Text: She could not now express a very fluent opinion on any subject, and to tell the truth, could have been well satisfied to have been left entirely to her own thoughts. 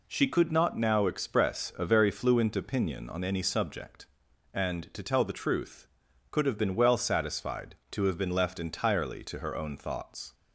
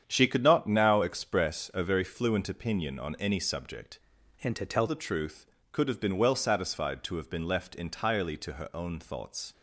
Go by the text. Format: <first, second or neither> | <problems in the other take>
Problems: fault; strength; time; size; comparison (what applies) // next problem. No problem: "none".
first | starts louder than the rest; strong; until 1.0 s; 8.5 dB // changes voice from "and" to "tell"; from 4.4 to 4.8 s; 0.4 s long